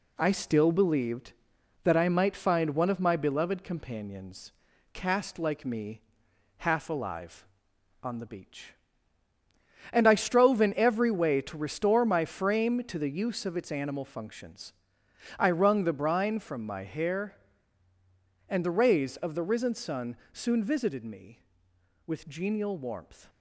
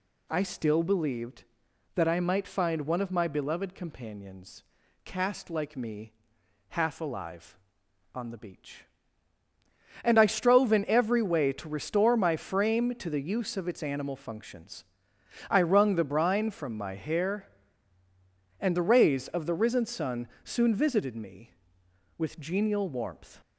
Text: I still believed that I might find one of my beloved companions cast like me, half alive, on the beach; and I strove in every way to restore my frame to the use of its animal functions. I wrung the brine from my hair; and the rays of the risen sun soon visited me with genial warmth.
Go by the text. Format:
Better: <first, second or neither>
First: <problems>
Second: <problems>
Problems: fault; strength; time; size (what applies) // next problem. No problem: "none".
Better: second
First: gets quieter; noticeable; throughout; 4 dB // pauses between "companions" and "cast"; at 4.5 s; 0.40 s long // pauses between "sun" and "soon"; slight; at 20.1 s; 0.16 s long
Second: pauses between "companions" and "cast"; at 4.6 s; 0.40 s long // pauses between "sun" and "soon"; slight; at 20.2 s; 0.16 s long